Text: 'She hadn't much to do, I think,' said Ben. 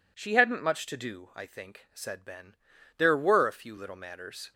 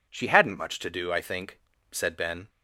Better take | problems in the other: second | goes on to say "There were a few little matters"; from 2.9 s on; 1.5 s long

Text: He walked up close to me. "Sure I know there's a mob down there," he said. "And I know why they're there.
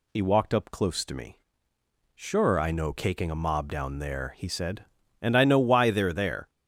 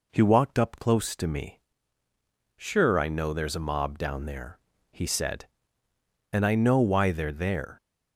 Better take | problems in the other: second | says "caking" for "there's"; at 2.9 s

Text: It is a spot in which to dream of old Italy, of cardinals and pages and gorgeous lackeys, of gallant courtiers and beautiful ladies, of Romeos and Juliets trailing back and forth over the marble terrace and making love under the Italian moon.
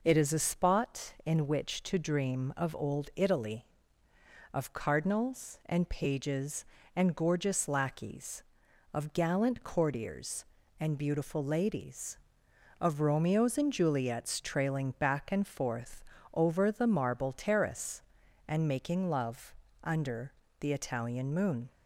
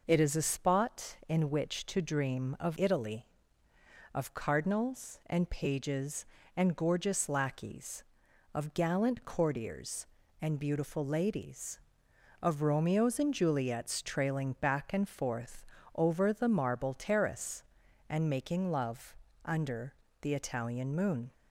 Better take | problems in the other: first | skips "old"; at 2.7 s // pauses between "forth" and "over"; slight; at 15.6 s; 0.30 s long; slight in the first // pauses between "love" and "under"; slight; at 19.1 s; 0.30 s long; slight in the first // pauses between "under" and "the"; slight; at 19.9 s; 0.30 s long; slight in the first

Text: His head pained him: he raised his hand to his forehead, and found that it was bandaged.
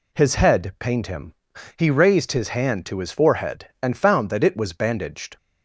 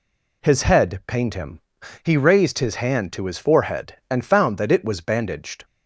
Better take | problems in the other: neither | none

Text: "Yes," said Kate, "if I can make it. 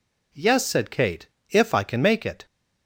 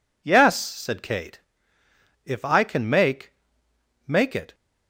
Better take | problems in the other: first | says "make" twice; at 4.0 s

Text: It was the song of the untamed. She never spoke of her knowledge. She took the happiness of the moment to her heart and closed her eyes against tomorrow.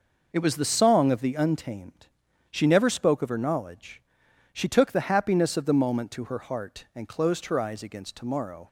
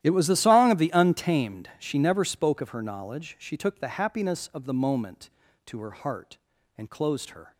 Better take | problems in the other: first | starts louder than the rest; strong; until 1.0 s; 12.5 dB // stops before "eyes against tomorrow"; at 7.5 s

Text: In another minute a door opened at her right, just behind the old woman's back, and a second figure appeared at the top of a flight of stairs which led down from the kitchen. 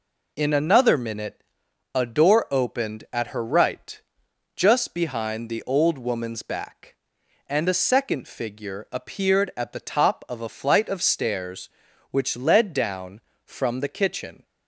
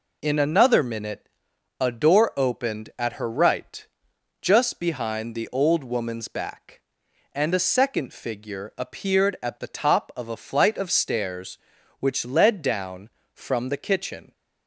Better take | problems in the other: neither | pauses between "minute" and "a"; noticeable; the same in both

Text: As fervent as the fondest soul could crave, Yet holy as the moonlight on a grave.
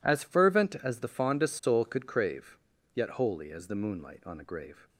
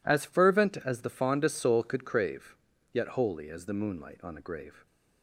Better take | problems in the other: neither | none

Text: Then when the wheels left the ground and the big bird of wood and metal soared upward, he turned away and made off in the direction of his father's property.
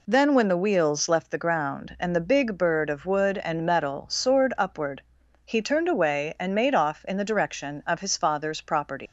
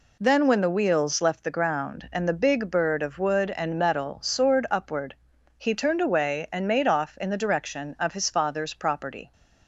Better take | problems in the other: second | leaves "property" unfinished; at 9.0 s; 135 ms

